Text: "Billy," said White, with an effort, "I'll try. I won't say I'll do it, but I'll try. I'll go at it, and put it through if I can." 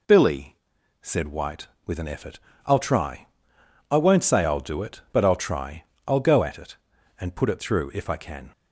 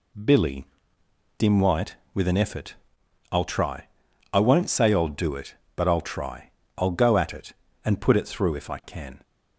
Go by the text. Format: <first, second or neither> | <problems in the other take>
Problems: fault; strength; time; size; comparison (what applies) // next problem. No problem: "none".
first | says "dim" for "said"; at 1.3 s